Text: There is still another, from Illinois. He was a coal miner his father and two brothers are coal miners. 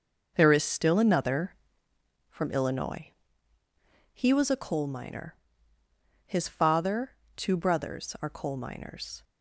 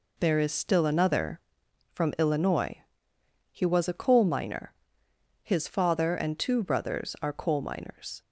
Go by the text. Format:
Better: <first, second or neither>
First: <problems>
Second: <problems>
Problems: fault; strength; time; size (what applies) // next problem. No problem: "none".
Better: second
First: pauses between "miner" and "his"; noticeable; at 5.3 s; 0.90 s long // skips "and"; at 7.2 s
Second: pauses between "miner" and "his"; noticeable; at 4.7 s; 0.70 s long